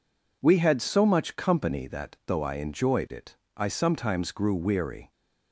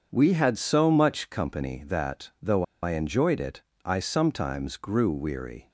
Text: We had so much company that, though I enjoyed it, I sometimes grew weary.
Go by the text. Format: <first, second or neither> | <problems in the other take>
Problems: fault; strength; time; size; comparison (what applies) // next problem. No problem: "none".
first | starts louder than the rest; until 1.1 s; 7 dB // pauses between "though" and "I"; slight; at 2.6 s; 0.19 s long